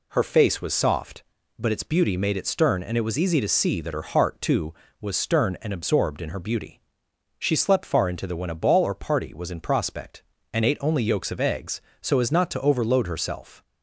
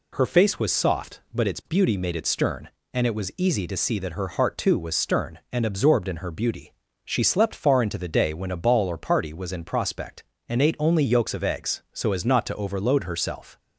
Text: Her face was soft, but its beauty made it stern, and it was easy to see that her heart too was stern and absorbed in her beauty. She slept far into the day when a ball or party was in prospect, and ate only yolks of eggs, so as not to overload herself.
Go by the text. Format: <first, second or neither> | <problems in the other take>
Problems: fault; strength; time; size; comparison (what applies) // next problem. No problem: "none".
second | skips "day"; at 8.3 s